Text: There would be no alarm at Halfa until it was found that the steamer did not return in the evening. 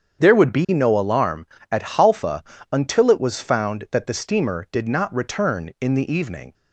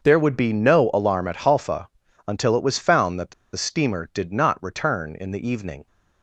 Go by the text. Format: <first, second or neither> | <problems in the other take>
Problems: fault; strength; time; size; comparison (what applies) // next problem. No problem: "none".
first | starts louder than the rest; until 1.0 s; 6.5 dB; strong in the first // pauses between "Halfa" and "until"; at 1.8 s; 0.40 s long; slight in the first // pauses between "the" and "steamer"; slight; at 3.3 s; 0.22 s long